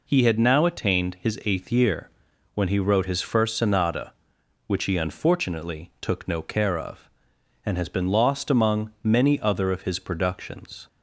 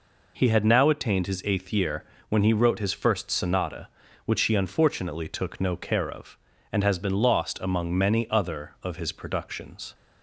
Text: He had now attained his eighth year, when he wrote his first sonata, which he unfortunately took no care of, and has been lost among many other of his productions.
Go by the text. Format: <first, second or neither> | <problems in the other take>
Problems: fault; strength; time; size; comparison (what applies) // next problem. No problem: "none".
neither | none